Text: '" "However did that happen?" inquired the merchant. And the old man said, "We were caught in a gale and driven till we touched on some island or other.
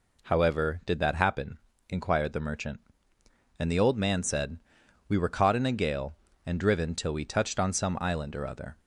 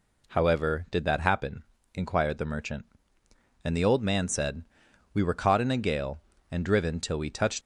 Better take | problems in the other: first | stops before "on some island or other"; at 7.6 s

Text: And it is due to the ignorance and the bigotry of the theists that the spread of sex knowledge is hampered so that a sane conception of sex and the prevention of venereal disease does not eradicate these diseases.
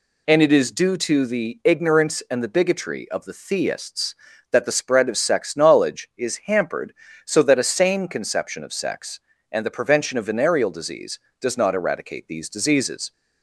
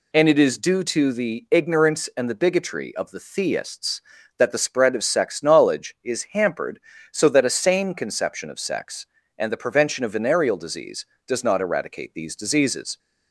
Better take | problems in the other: neither | none

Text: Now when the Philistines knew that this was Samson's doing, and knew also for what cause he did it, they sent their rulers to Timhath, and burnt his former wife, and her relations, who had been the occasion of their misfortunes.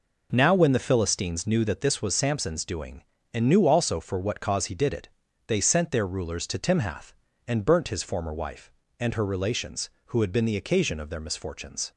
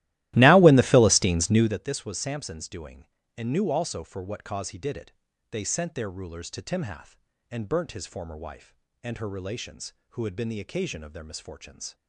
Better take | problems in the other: first | starts louder than the rest; strong; until 1.8 s; 16 dB

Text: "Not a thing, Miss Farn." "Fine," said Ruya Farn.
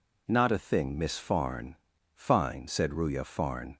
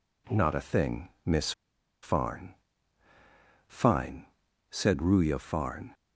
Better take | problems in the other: first | pauses between "Miss" and "Farn"; noticeable; at 1.5 s; 0.51 s long

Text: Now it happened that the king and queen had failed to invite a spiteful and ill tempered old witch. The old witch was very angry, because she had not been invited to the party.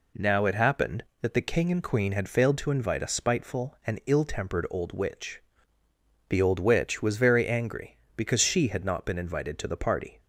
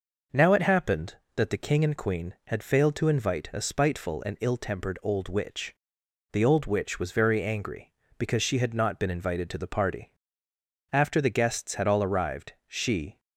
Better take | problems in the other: first | goes on to say "After the guests had all arrived she"; strong; from 10.9 s on; 2.2 s long

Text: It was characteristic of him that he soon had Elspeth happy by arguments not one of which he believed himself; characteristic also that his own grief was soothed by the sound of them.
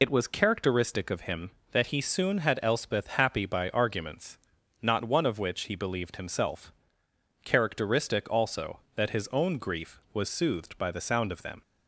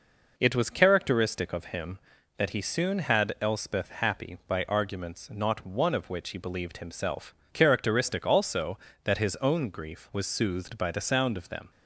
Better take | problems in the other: second | loses the start of "It"; at 0.0 s; 60 ms // pauses between "arguments" and "not"; at 4.3 s; 0.44 s long

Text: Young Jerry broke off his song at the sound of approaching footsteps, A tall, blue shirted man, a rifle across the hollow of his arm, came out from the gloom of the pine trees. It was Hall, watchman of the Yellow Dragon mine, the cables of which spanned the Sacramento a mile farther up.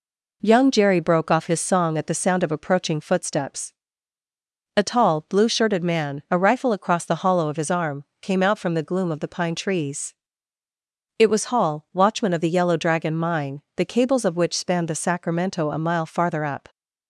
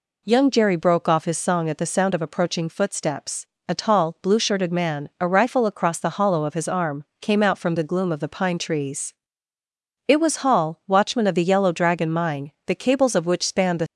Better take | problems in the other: first | stops before "Sacramento a mile farther up"; at 13.8 s

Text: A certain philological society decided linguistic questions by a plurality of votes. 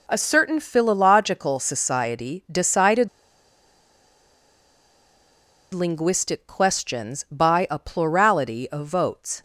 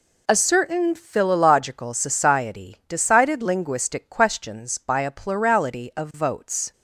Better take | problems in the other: second | pauses between "decided" and "linguistic"; strong; at 3.0 s; 2.6 s long

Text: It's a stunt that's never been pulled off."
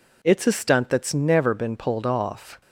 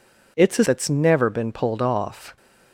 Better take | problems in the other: first | skips "stunt"; at 0.6 s

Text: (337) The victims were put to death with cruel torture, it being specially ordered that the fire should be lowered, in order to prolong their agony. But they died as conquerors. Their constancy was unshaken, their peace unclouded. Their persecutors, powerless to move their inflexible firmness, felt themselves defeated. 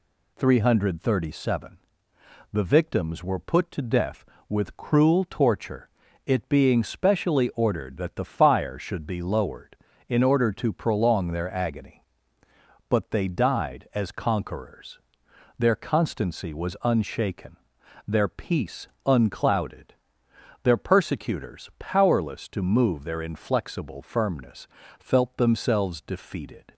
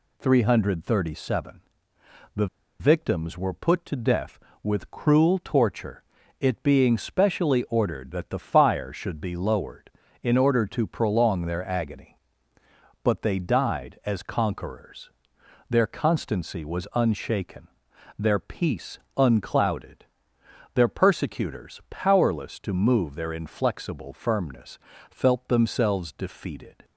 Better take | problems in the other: first | pauses between "The" and "victims"; slight; at 2.4 s; 0.33 s long // pauses between "peace" and "unclouded"; slight; at 18.9 s; 0.20 s long; slight in the first

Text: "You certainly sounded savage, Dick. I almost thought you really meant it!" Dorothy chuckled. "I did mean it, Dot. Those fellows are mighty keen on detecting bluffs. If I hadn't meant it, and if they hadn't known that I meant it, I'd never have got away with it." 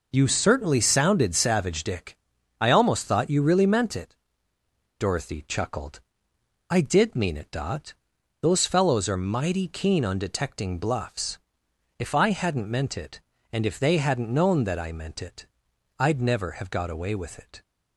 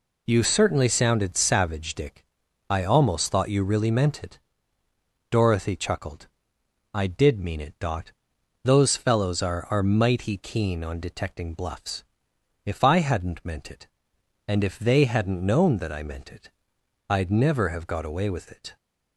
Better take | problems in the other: first | says "are" twice; at 9.6 s

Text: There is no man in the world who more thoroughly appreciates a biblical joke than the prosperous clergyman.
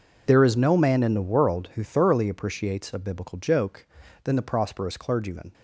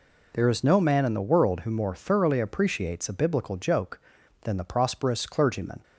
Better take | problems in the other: second | skips "more"; at 1.8 s

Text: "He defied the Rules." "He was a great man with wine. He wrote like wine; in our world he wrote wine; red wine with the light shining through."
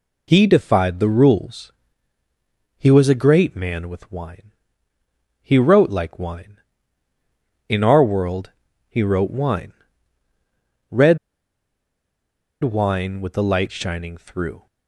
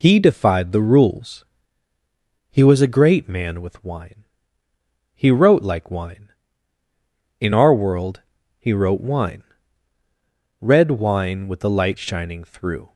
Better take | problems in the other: second | pauses between "world" and "he"; slight; at 8.5 s; 0.36 s long; slight in the second // pauses between "red" and "wine"; strong; at 11.1 s; 1.4 s long

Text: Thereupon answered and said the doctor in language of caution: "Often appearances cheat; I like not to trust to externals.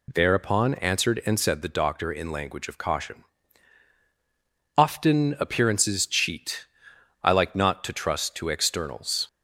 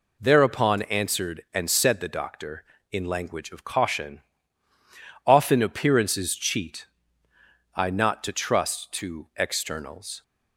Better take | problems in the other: first | skips "like"; at 7.8 s

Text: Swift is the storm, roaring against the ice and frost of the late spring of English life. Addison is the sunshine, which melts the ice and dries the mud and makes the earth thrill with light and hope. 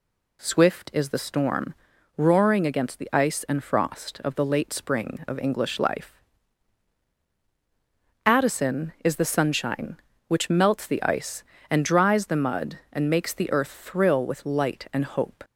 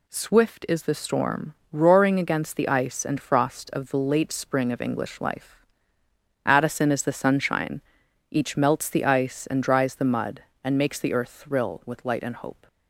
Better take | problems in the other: first | says "each" for "which"; at 8.3 s

